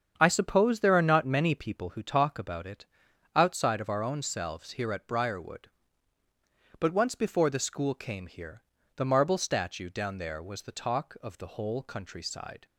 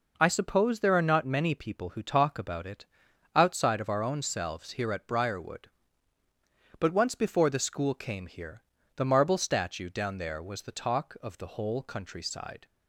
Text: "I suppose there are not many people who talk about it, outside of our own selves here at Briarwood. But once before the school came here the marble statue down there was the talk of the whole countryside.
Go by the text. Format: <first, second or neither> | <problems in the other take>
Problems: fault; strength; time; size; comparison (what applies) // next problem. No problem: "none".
second | starts louder than the rest; strong; until 2.0 s; 7.5 dB // pauses between "here" and "the"; slight; at 8.6 s; 0.32 s long; slight in the second